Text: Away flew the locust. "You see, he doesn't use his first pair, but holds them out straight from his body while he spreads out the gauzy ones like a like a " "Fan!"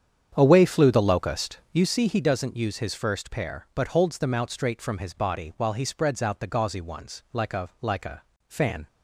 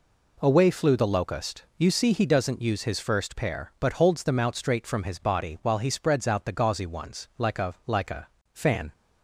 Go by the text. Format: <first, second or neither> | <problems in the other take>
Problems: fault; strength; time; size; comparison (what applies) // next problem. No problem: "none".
second | starts louder than the rest; strong; until 1.9 s; 8.5 dB